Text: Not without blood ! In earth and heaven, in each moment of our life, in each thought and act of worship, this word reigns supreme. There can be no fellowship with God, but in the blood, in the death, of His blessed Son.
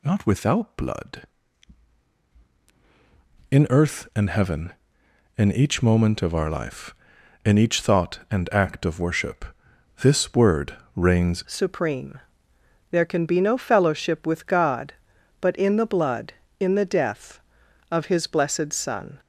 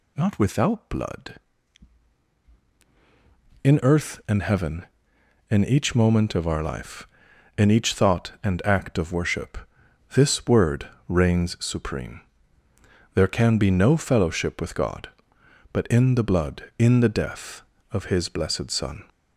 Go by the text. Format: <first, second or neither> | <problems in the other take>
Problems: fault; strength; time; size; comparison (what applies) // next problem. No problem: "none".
second | pauses between "word" and "reigns"; slight; at 10.7 s; 0.20 s long; slight in the second // changes voice at "supreme"; from 11.4 s on; 7.7 s long